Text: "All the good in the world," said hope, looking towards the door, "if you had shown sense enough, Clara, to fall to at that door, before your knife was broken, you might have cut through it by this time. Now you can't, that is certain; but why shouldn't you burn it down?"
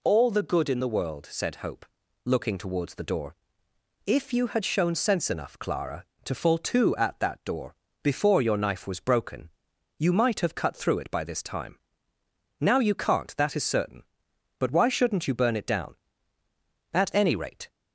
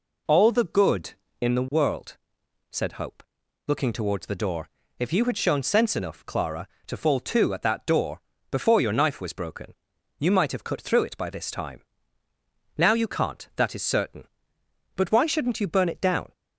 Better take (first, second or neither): second